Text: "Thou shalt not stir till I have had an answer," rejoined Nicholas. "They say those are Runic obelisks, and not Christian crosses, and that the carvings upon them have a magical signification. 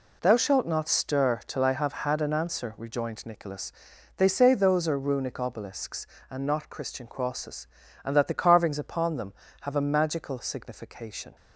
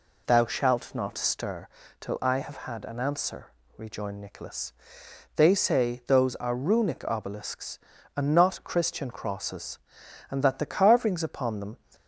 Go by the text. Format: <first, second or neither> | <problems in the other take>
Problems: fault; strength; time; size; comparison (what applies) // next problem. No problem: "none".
first | pauses between "stir" and "till"; slight; at 1.6 s; 0.32 s long // stops before "have a magical signification"; at 11.9 s